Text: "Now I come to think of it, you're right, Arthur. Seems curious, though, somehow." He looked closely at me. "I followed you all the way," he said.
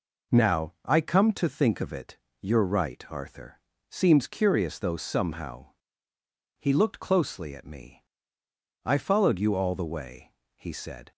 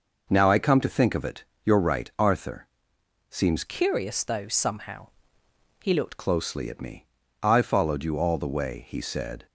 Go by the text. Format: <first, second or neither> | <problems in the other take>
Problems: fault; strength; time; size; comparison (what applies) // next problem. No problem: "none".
first | changes voice from "curious" to "looked"; from 3.6 to 6.1 s; 2.5 s long